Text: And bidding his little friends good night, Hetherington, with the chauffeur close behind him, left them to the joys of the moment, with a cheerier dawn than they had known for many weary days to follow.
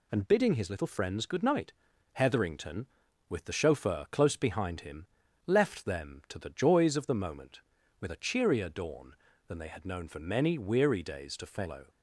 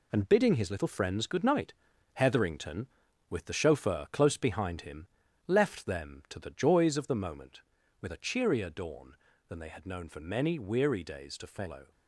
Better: first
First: none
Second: gets quieter; strong; throughout; 7.5 dB

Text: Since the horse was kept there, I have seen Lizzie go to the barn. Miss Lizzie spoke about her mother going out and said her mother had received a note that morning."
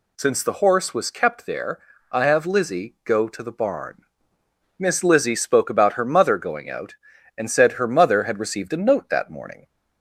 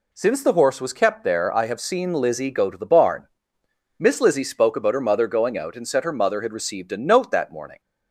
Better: second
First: skips "seen"; at 2.4 s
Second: none

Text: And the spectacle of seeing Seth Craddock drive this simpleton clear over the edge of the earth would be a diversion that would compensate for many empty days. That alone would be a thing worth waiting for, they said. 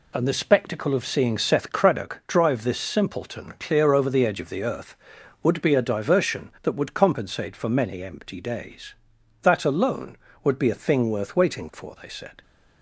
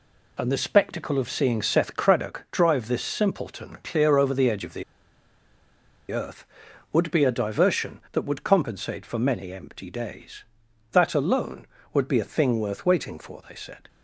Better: first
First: none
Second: pauses between "the" and "earth"; strong; at 4.8 s; 1.2 s long

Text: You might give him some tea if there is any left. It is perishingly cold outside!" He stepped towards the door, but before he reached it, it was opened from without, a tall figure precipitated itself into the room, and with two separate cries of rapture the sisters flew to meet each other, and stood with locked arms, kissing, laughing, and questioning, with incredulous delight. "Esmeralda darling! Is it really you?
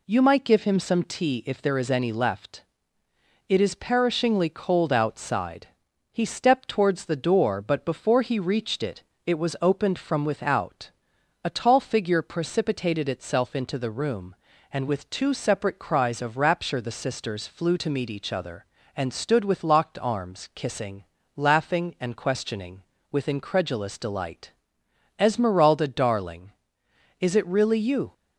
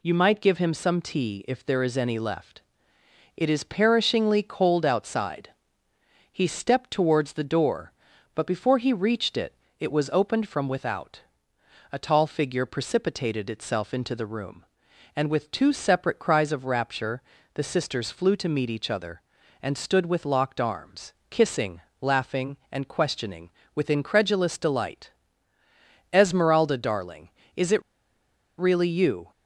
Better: first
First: none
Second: pauses between "rapture" and "the"; slight; at 17.2 s; 0.32 s long // pauses between "it" and "really"; noticeable; at 27.8 s; 0.76 s long

